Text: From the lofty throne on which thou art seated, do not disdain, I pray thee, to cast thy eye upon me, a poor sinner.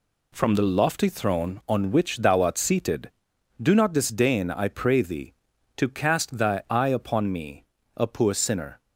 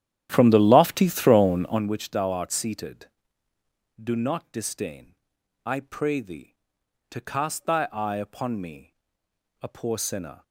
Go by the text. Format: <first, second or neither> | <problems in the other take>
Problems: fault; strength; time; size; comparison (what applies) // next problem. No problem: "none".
first | starts louder than the rest; strong; until 1.9 s; 11 dB